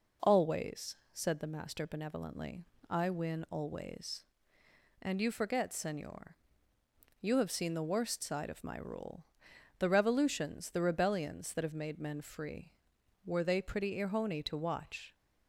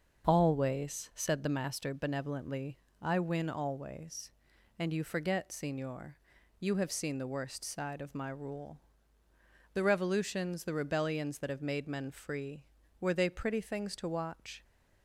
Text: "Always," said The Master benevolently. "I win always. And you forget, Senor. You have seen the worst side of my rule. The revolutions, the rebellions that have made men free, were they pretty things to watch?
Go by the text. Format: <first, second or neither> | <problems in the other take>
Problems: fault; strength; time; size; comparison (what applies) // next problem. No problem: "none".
second | says "irhoni" for "things"; at 13.9 s